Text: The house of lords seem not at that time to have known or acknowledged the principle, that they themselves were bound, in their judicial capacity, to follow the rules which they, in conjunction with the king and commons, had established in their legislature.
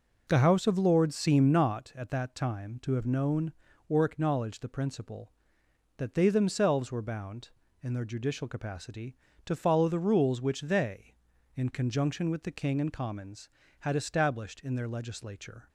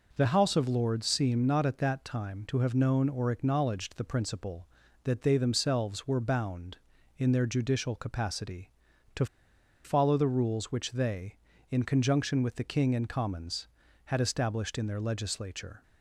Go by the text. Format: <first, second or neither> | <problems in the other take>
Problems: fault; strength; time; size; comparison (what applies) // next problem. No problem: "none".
first | pauses between "to" and "follow"; noticeable; at 9.2 s; 0.59 s long